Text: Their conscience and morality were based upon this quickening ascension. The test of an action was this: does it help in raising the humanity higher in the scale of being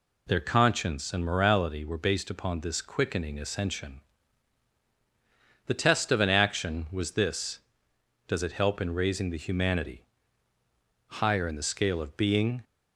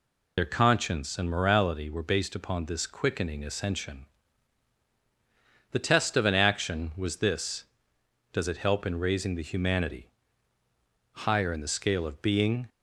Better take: first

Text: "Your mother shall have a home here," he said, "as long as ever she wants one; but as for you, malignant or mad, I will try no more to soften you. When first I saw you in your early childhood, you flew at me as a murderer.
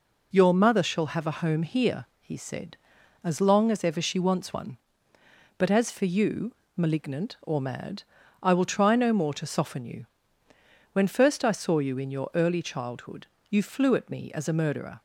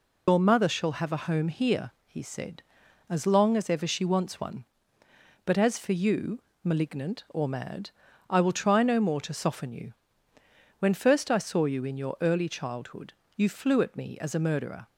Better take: first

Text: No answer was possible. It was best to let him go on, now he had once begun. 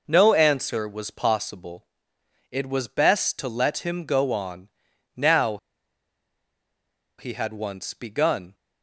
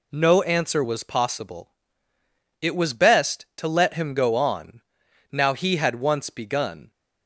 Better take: second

